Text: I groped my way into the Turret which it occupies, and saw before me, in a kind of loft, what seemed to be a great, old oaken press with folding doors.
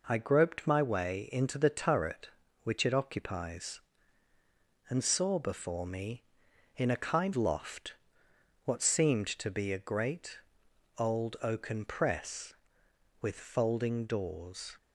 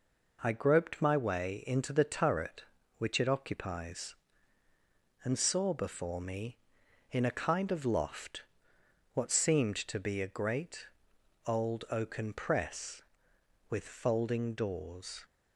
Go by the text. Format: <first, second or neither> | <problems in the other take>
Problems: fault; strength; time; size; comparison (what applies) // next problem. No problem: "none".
second | skips "of"; at 7.3 s